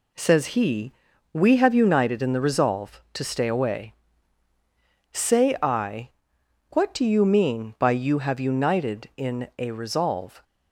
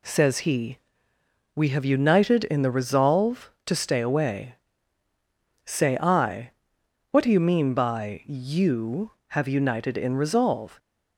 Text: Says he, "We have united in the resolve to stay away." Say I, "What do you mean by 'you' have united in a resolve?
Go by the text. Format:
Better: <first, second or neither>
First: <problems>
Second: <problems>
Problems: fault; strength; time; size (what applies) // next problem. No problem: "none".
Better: first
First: none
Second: skips "a"; at 10.1 s